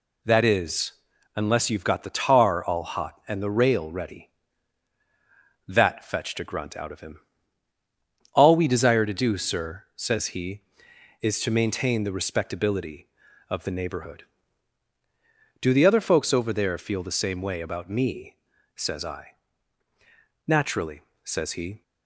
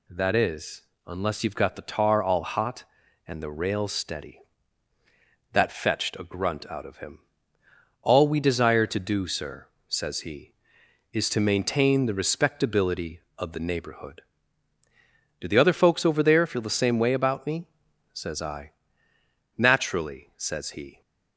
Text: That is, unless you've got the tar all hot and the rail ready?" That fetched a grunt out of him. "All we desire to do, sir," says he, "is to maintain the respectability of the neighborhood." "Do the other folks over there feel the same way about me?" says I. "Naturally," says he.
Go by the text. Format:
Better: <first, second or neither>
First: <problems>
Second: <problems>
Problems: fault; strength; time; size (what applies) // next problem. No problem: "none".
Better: first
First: none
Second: says "steady" for "ready"; at 3.8 s